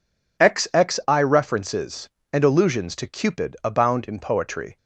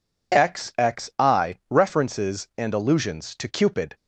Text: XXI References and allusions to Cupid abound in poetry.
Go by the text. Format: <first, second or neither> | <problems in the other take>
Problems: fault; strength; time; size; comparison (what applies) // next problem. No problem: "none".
first | stops before "abound in poetry"; at 3.9 s